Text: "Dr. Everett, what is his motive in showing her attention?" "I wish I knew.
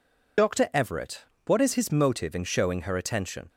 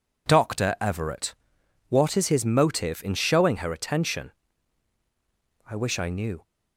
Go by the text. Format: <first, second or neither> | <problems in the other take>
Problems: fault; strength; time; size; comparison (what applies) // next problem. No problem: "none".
second | stops before "I wish I knew"; at 3.4 s